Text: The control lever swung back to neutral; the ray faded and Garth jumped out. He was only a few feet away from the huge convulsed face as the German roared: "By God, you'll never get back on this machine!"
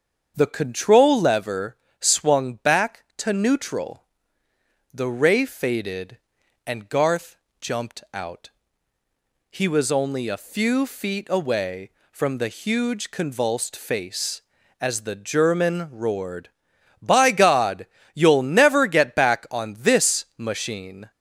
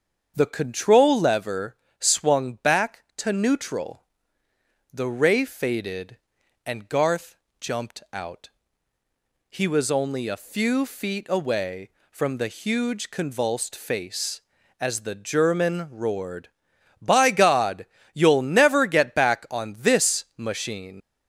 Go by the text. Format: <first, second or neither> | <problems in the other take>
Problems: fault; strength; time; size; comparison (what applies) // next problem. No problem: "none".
first | starts louder than the rest; until 1.3 s; 7 dB; strong in the first // pauses between "lever" and "swung"; slight; at 1.7 s; 0.24 s long; slight in the first // pauses between "Garth" and "jumped"; slight; at 7.3 s; 0.24 s long; slight in the first // leaves "machine" unfinished; at 21.0 s; 95 ms